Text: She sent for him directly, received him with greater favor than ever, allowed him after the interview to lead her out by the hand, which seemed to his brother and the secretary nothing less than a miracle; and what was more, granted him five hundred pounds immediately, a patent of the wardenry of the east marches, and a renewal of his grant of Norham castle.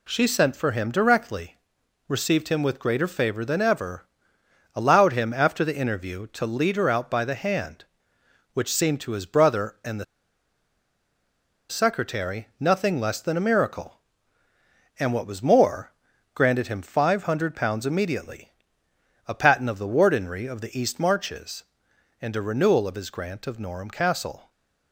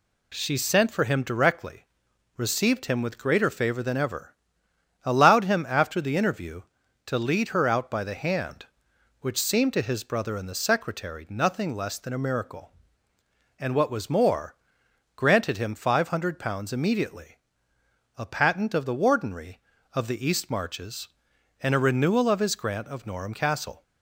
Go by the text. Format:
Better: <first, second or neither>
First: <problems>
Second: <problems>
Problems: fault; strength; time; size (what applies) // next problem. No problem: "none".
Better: second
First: pauses between "the" and "secretary"; strong; at 10.0 s; 1.6 s long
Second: none